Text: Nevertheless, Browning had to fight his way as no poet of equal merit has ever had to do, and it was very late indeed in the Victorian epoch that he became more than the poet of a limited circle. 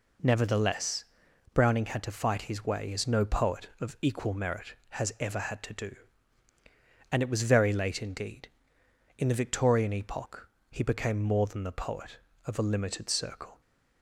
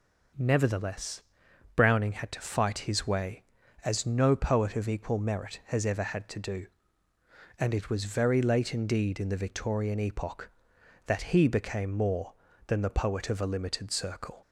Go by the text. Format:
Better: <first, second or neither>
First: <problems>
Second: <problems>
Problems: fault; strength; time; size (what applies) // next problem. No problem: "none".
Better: second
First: skips "that"; at 10.5 s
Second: none